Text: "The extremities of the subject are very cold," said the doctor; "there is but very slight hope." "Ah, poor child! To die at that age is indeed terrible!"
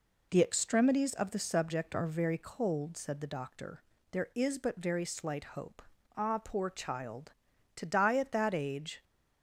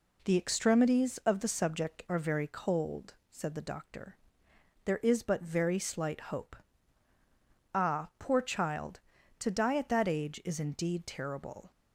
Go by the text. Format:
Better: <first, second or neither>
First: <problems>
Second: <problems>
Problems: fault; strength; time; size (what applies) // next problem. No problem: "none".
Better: second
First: stops before "is indeed terrible"; at 9.0 s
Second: none